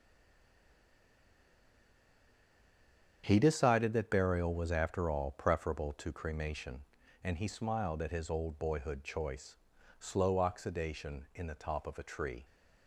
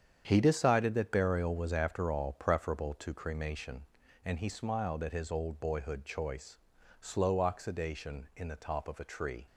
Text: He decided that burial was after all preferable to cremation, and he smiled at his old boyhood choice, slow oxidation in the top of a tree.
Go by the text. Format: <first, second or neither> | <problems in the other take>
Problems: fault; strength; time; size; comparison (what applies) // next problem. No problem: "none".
second | stays silent before the first word; strong; until 3.2 s; 3.2 s long // starts louder than the rest; strong; until 4.2 s; 8 dB; strong in the second